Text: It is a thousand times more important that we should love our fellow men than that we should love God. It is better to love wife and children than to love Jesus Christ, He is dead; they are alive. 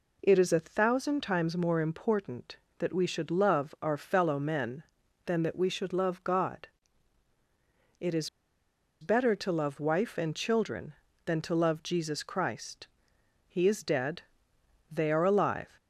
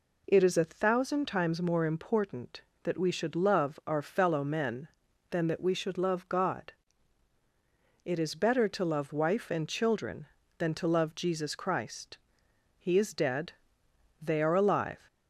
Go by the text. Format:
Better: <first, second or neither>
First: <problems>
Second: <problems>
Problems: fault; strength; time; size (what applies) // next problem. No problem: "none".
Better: second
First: pauses between "is" and "better"; noticeable; at 8.2 s; 0.72 s long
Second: none